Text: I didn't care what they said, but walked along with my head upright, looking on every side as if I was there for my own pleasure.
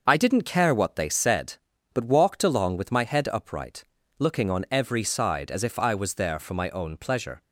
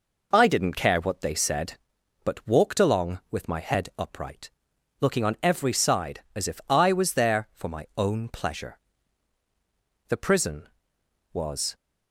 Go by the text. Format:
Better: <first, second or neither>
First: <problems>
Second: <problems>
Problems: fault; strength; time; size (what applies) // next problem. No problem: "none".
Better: first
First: none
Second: goes on to say "The prison was"; strong; from 10.0 s on; 1.6 s long